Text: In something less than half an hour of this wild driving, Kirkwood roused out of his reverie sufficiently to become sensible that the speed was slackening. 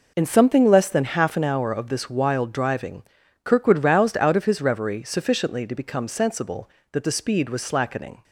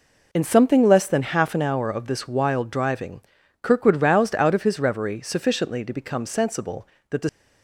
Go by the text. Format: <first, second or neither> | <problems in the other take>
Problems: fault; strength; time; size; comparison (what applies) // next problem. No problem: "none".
first | stops before "speed was slackening"; at 7.2 s